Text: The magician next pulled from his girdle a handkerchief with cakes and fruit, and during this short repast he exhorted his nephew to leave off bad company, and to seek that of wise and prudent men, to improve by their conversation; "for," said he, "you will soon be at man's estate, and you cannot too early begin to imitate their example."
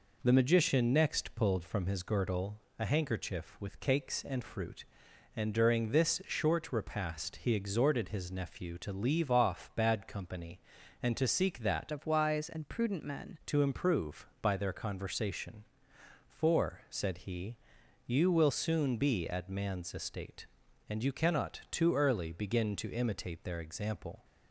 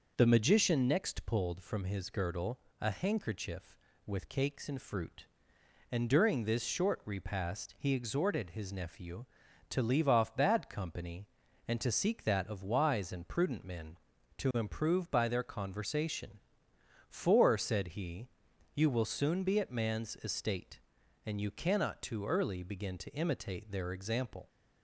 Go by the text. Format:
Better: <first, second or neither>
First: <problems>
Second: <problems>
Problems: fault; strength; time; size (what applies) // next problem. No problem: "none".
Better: second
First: pauses between "girdle" and "a"; slight; at 2.6 s; 0.18 s long // changes voice from "of" to "men"; from 11.9 to 13.3 s; 1.4 s long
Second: pauses between "girdle" and "a"; slight; at 2.5 s; 0.22 s long